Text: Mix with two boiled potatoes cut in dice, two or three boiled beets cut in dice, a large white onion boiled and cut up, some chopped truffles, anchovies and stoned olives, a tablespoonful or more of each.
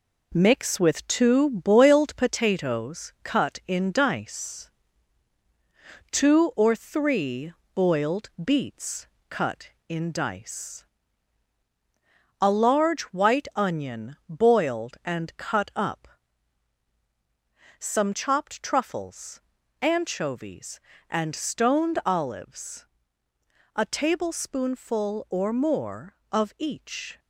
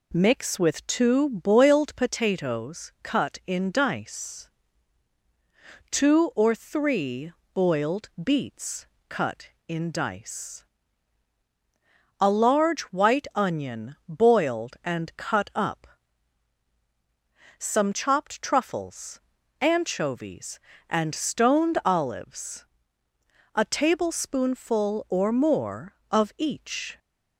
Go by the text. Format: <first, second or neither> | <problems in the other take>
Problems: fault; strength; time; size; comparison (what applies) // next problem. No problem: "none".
second | gets quieter; noticeable; throughout; 5.5 dB // pauses between "three" and "boiled"; slight; at 7.5 s; 0.22 s long; slight in the second // pauses between "beets" and "cut"; slight; at 9.0 s; 0.24 s long; slight in the second